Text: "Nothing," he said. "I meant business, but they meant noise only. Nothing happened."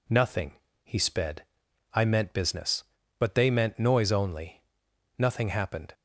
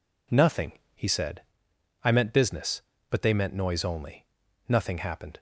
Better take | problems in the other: second | says "sped" for "said"; at 1.0 s

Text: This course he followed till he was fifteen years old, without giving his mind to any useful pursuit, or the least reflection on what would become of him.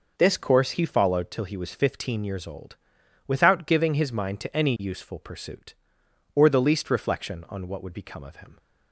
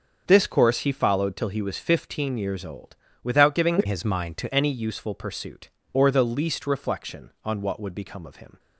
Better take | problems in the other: first | starts louder than the rest; until 1.2 s; 6.5 dB // changes voice from "his" to "to"; from 3.8 to 4.5 s; 0.7 s long

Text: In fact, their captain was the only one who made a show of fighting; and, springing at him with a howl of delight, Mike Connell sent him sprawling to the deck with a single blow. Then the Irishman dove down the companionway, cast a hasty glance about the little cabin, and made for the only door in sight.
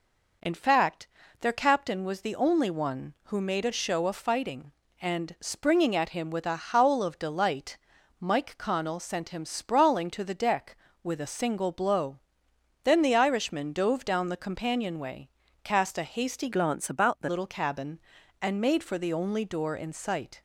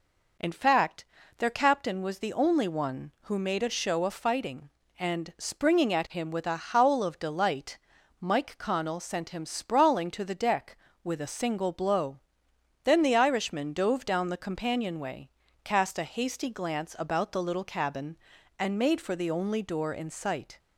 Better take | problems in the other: second | changes voice from "glance" to "the"; from 16.5 to 17.2 s; 0.7 s long

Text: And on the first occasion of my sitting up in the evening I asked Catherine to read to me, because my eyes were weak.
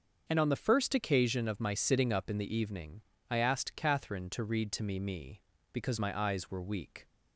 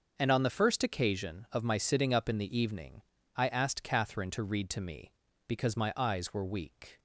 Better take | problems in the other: second | starts louder than the rest; until 1.2 s; 6.5 dB; also in the second // pauses between "evening" and "I"; slight; at 3.0 s; 0.28 s long; slight in the second // says "me" twice; at 4.9 s

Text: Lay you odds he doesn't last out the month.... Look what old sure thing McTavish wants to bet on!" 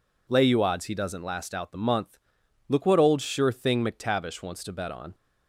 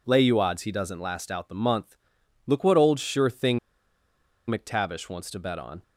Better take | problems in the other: first | pauses between "thing" and "McTavish"; noticeable; at 3.5 s; 0.89 s long

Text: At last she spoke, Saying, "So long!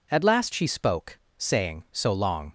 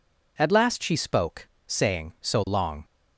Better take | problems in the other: neither | none

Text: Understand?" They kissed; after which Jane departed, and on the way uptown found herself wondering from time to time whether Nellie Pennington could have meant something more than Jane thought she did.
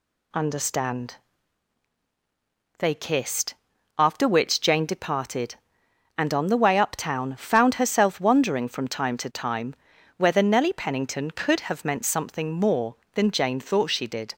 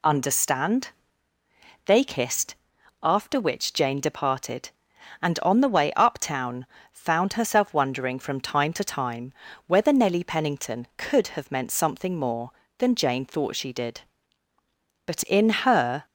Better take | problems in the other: first | pauses between "uptown" and "found"; slight; at 6.6 s; 0.26 s long // pauses between "time" and "whether"; slight; at 9.3 s; 0.32 s long; also in the first // goes on to say "But in her"; noticeable; from 15.0 s on; 1.0 s long

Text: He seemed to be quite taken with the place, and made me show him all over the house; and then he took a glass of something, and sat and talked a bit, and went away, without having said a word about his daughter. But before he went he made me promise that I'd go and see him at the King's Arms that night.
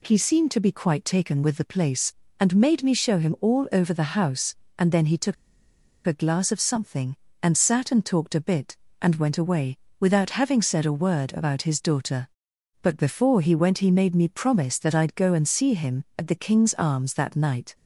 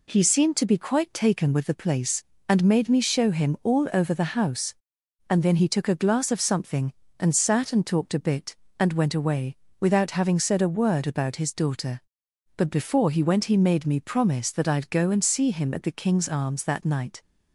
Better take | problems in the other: second | pauses between "took" and "a"; noticeable; at 5.3 s; 0.72 s long

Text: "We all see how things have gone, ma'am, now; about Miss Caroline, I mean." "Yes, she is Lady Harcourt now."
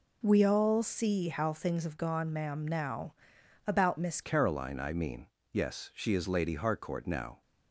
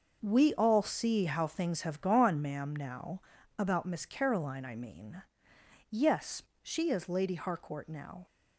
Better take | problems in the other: second | changes voice at "Caroline"; from 4.2 s on; 3.2 s long

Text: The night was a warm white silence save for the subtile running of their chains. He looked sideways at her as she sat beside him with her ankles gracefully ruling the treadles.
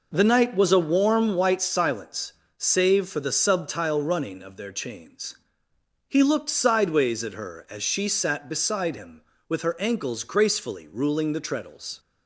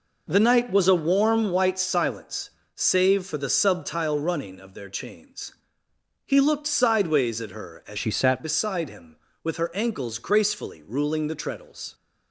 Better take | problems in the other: first | pauses between "silence" and "save"; slight; at 2.5 s; 0.24 s long; slight in the first // changes voice from "she" to "sat"; from 7.9 to 8.4 s; 0.5 s long

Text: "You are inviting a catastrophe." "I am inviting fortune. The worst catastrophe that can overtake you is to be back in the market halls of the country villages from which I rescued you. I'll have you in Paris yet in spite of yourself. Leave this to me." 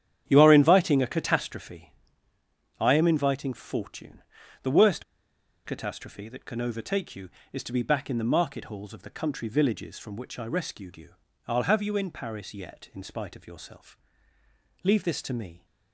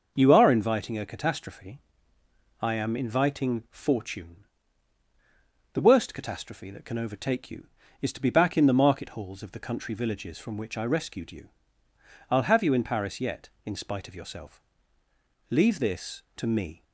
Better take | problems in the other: second | starts louder than the rest; strong; until 1.2 s; 9.5 dB; noticeable in the second // pauses between "worst" and "catastrophe"; noticeable; at 5.0 s; 0.62 s long

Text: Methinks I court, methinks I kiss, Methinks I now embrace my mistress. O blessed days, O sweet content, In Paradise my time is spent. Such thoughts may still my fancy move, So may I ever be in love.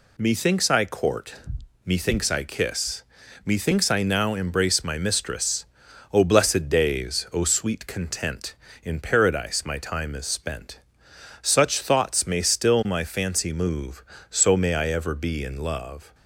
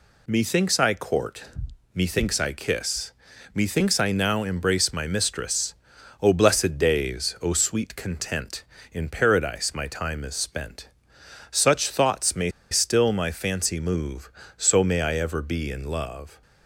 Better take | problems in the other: first | pauses between "may" and "still"; slight; at 12.5 s; 0.20 s long

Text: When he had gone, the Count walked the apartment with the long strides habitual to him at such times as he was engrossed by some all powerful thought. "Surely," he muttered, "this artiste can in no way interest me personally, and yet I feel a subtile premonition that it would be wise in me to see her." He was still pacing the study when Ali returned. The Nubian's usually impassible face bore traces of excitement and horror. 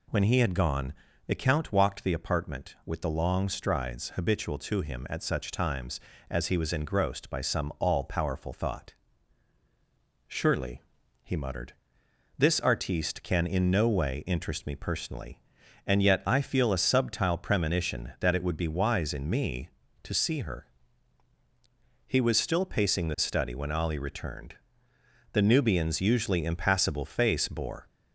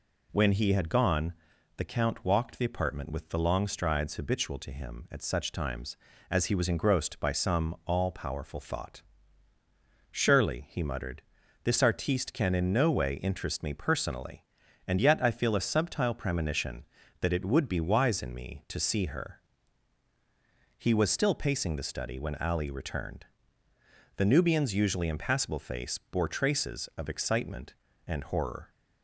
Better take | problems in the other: second | stops before "traces of excitement and horror"; at 27.8 s

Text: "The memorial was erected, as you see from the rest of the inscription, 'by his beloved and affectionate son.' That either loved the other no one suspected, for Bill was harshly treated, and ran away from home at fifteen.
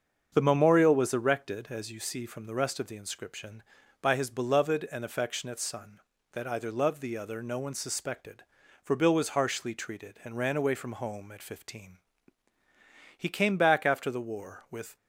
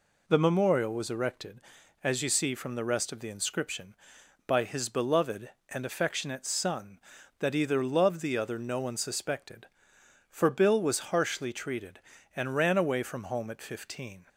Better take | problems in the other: second | starts louder than the rest; until 1.3 s; 7 dB // goes on to say "He came back after the war with"; strong; from 13.1 s on; 1.7 s long

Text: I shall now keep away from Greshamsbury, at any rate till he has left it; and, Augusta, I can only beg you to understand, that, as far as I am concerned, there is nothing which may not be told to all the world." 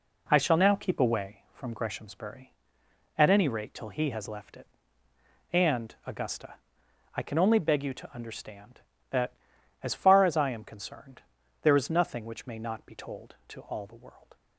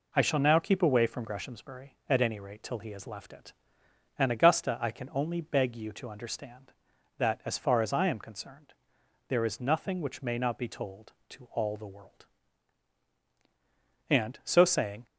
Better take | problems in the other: first | goes on to say "And so saying"; noticeable; from 14.0 s on; 0.96 s long

